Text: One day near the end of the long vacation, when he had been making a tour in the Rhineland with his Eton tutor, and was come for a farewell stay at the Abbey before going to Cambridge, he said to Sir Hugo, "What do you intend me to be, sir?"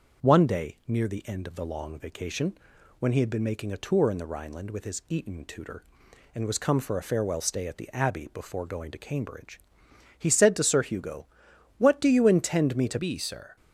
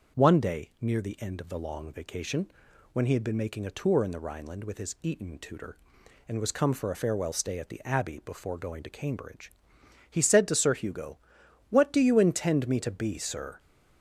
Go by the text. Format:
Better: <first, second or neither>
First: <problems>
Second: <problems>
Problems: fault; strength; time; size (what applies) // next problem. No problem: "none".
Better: second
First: starts louder than the rest; until 1.3 s; 6.5 dB // changes voice at "be"; from 12.9 s on; 0.6 s long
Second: starts louder than the rest; until 1.2 s; 6.5 dB